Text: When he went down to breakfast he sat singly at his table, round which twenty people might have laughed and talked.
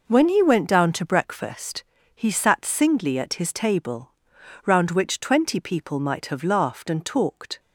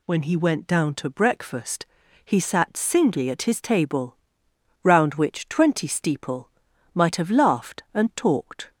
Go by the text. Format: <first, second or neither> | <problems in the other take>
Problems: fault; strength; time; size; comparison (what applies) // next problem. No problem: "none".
first | pauses between "breakfast" and "he"; at 1.8 s; 0.40 s long; slight in the first // says "steeple" for "people"; at 5.8 s